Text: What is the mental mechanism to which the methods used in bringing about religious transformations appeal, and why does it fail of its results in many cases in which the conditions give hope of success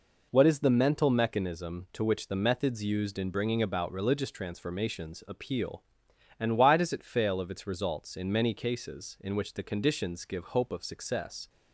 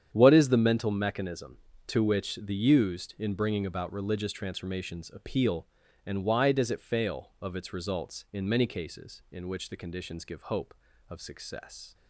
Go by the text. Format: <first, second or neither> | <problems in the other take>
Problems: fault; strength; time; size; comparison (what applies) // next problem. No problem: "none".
first | starts louder than the rest; strong; until 1.1 s; 9 dB // skips "methods"; at 2.5 s